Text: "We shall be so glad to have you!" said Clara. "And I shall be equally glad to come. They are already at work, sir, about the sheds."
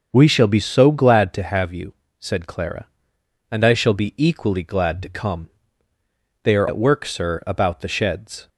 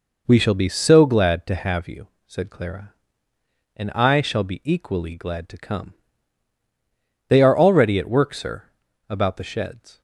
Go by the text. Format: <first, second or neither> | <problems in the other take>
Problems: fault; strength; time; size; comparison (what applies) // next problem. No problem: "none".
second | starts louder than the rest; until 1.1 s; 6.5 dB // skips "already"; at 6.6 s